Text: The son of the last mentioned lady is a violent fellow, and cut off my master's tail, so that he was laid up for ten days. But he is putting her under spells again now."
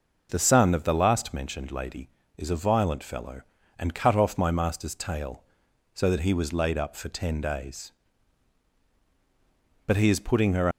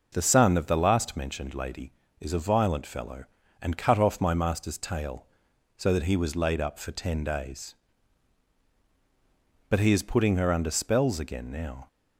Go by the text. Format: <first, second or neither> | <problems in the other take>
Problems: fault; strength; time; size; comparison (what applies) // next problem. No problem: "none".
second | stops before "under spells again now"; at 10.7 s